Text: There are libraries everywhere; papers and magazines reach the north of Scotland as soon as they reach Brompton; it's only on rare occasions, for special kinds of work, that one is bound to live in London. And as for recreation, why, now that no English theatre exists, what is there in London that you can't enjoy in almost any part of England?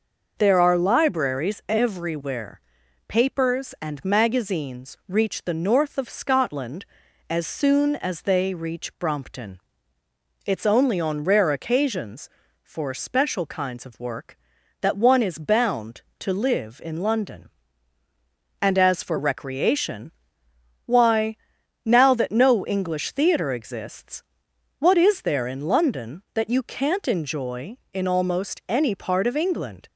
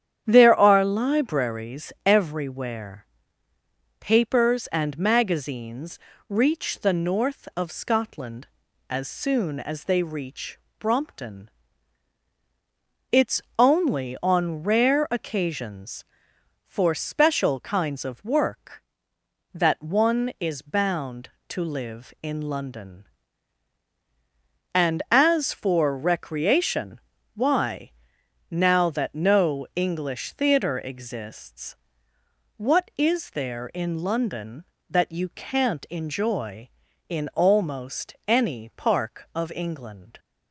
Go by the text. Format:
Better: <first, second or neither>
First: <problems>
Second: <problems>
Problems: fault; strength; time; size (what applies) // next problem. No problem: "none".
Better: first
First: none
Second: starts louder than the rest; strong; until 1.2 s; 9.5 dB // pauses between "libraries" and "everywhere"; slight; at 1.9 s; 0.16 s long // pauses between "magazines" and "reach"; slight; at 5.9 s; 0.30 s long // pauses between "reach" and "Brompton"; slight; at 10.5 s; 0.20 s long // pauses between "it's" and "only"; slight; at 13.4 s; 0.18 s long // says "park" for "part"; at 38.7 s